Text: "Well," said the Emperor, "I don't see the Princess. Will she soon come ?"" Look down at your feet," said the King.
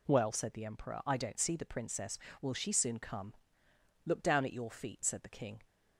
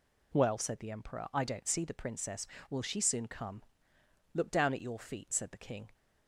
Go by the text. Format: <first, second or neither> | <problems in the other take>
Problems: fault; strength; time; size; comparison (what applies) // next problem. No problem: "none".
neither | none